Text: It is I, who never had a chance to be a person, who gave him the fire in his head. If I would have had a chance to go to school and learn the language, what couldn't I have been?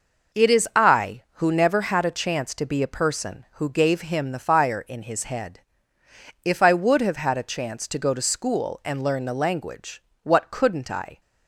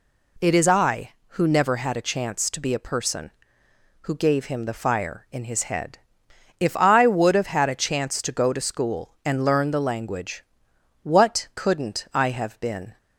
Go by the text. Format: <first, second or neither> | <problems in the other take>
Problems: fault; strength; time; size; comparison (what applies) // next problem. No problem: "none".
second | stops before "have been"; at 11.2 s